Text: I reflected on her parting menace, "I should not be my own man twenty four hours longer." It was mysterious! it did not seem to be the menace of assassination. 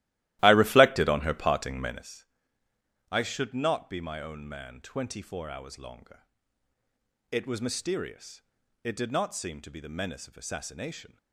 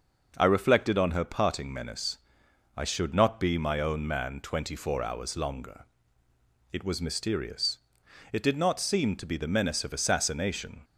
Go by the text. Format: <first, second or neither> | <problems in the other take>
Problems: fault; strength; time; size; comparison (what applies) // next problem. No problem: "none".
second | starts louder than the rest; strong; until 2.2 s; 16 dB